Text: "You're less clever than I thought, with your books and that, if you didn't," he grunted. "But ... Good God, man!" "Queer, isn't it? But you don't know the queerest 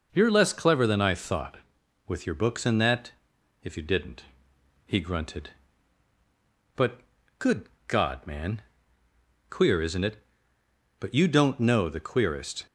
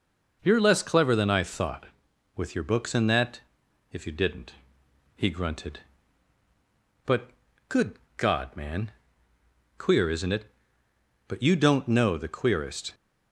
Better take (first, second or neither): neither